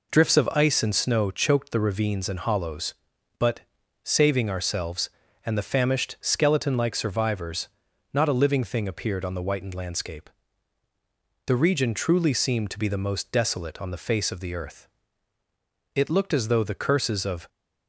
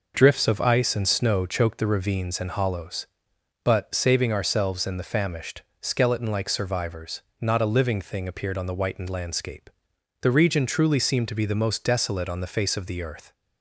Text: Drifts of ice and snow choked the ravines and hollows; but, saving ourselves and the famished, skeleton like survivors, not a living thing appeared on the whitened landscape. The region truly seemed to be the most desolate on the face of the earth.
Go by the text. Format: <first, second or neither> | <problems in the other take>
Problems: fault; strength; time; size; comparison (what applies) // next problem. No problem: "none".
second | goes on to say "It looked as though the curses of"; from 15.9 s on; 1.5 s long